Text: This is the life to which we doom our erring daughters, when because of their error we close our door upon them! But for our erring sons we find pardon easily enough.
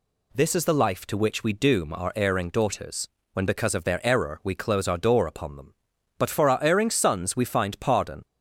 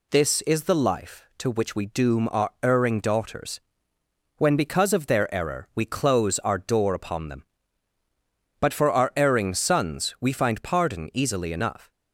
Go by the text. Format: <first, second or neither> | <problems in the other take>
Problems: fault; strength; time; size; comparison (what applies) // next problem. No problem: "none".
second | stops before "easily enough"; at 8.2 s